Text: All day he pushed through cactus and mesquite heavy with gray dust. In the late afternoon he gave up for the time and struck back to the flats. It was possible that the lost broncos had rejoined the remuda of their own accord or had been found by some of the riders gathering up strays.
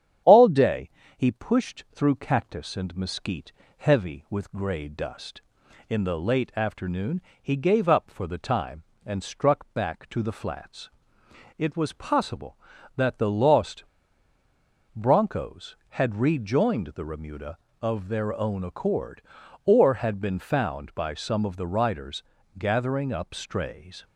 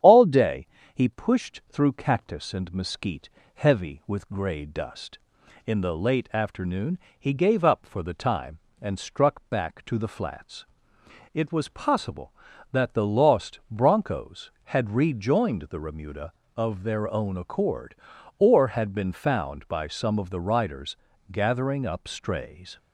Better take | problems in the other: second | starts louder than the rest; strong; until 1.5 s; 9 dB; strong in the second // pauses between "day" and "he"; slight; at 0.8 s; 0.28 s long; slight in the second // pauses between "mesquite" and "heavy"; slight; at 3.5 s; 0.26 s long; slight in the second // pauses between "afternoon" and "he"; slight; at 7.1 s; 0.22 s long; slight in the second // pauses between "lost" and "broncos"; at 13.8 s; 1.1 s long // pauses between "riders" and "gathering"; slight; at 22.2 s; 0.36 s long; slight in the second

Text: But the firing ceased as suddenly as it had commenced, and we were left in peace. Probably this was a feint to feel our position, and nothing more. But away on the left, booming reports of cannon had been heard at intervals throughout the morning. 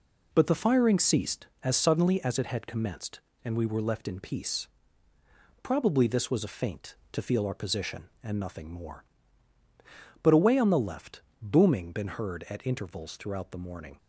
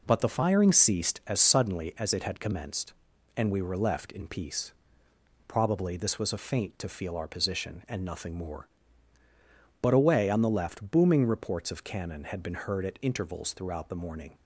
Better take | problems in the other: second | skips "reports of cannon had"; at 11.9 s

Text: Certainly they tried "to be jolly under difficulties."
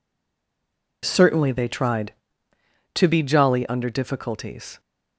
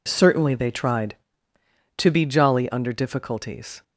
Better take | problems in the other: second | stays silent before the first word; until 1.0 s; 1.0 s long

